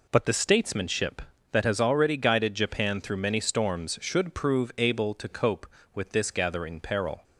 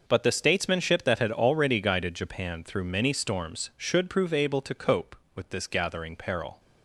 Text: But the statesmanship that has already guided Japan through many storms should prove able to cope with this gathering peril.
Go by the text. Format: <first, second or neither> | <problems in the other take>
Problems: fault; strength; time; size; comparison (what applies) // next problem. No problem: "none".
first | says "had" for "has"; at 1.1 s